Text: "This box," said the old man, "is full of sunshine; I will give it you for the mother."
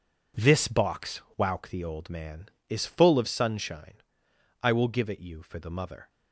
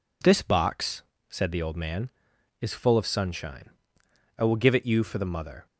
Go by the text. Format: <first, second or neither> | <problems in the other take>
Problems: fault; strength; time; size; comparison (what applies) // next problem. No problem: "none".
second | says "wauk" for "said"; at 1.3 s